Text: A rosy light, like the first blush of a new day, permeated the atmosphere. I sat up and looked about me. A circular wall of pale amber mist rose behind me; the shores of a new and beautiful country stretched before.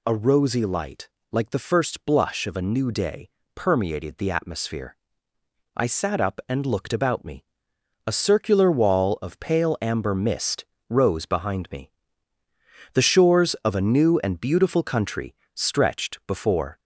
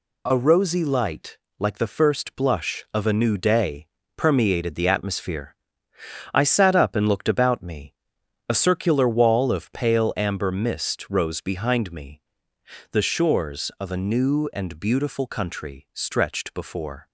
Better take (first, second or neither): second